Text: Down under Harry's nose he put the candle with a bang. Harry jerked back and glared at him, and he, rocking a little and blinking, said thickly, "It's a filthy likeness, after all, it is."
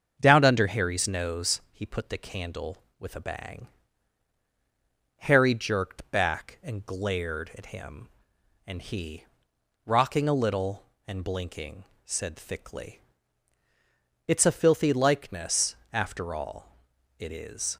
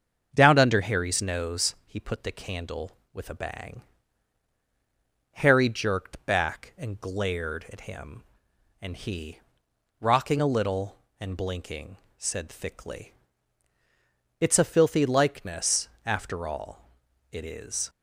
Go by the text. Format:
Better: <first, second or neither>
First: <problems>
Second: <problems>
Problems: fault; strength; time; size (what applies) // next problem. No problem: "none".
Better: neither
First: starts louder than the rest; until 1.2 s; 7 dB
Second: starts louder than the rest; until 1.3 s; 7 dB